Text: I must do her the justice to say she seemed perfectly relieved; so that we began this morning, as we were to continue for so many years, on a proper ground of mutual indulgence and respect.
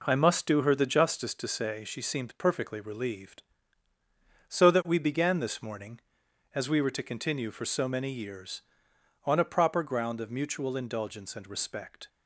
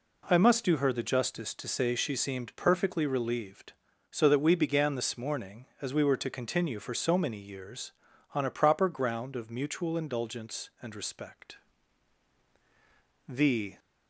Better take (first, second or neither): first